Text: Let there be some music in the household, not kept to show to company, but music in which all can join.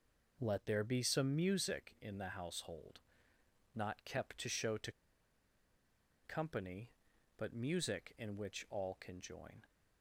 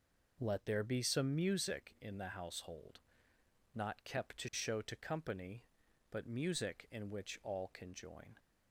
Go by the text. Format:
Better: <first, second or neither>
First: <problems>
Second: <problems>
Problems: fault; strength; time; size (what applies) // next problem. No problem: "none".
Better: second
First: pauses between "to" and "company"; strong; at 4.9 s; 1.3 s long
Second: none